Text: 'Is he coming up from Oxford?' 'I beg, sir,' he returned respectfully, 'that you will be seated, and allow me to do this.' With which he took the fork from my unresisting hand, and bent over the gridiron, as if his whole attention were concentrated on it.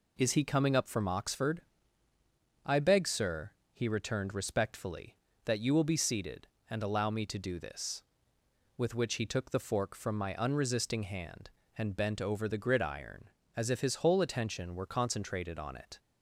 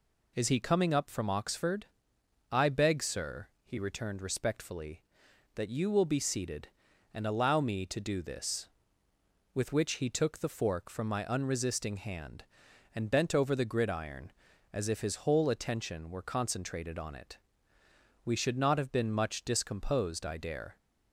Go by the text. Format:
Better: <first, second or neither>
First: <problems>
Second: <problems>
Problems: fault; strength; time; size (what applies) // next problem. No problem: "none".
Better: first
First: none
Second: goes on to say "We should not have been much discomposed I dare"; strong; from 18.2 s on; 2.5 s long